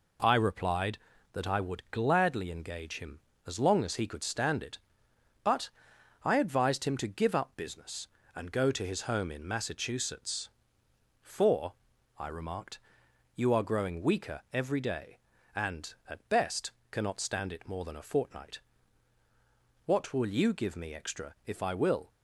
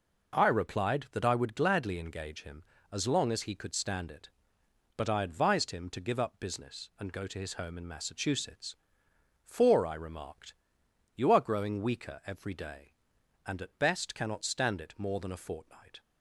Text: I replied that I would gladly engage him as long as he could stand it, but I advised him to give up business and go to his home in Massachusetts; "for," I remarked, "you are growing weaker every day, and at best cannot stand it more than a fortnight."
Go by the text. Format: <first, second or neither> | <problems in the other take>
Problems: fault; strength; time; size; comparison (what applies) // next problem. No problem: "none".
second | pauses between "but" and "I"; noticeable; at 5.7 s; 0.52 s long // pauses between "best" and "cannot"; slight; at 16.7 s; 0.20 s long // goes on to say "What will you give me extra if I will"; strong; from 19.8 s on; 2.2 s long